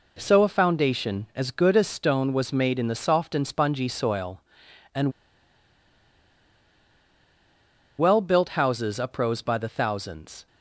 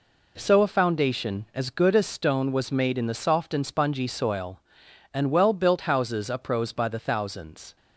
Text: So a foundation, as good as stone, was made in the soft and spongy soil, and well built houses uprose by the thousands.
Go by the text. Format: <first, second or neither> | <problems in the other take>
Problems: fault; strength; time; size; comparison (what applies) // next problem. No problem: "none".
second | pauses between "and" and "well"; strong; at 5.1 s; 2.8 s long